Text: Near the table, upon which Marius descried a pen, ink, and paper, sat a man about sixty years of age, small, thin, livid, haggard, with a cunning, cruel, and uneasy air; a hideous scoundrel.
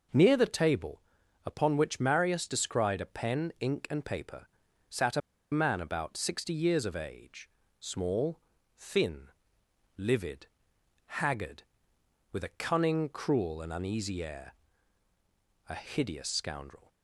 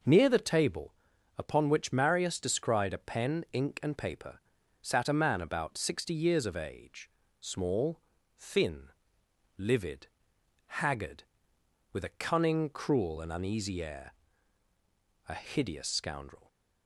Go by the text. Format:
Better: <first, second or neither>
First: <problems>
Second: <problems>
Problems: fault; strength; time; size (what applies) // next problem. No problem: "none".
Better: second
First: pauses between "a" and "man"; slight; at 5.2 s; 0.31 s long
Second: none